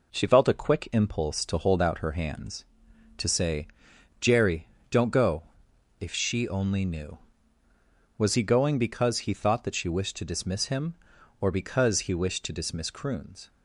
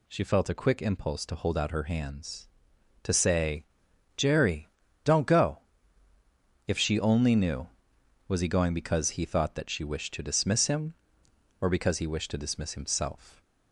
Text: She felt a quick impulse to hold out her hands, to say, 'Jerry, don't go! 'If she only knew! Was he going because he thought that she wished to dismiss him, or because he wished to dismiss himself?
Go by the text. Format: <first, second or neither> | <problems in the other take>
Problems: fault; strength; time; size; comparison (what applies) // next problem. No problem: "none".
second | says "croons" for "himself"; at 12.9 s